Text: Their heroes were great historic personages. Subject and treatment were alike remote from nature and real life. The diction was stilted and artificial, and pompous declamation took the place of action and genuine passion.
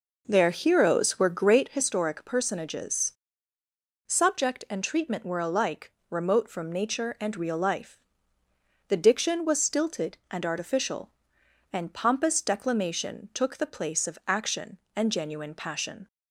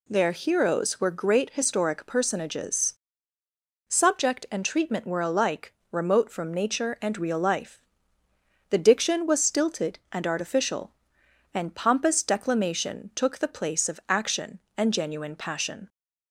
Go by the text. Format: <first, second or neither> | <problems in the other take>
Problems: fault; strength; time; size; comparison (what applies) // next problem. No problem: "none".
second | starts louder than the rest; noticeable; until 1.9 s; 4.5 dB // pauses between "alike" and "remote"; slight; at 5.9 s; 0.18 s long; slight in the second